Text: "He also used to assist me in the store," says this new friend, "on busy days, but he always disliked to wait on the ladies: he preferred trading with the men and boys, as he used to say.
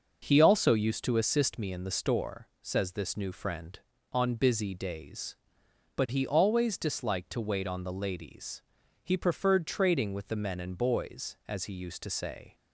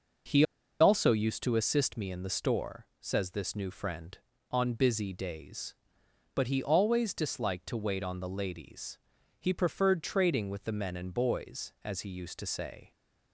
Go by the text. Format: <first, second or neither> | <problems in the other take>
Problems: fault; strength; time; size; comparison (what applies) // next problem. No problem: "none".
first | pauses between "He" and "also"; at 0.4 s; 0.37 s long